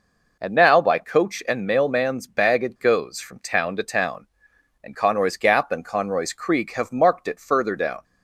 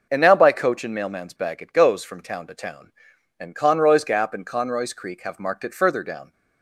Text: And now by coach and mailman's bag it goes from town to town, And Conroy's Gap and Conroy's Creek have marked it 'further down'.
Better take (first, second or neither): neither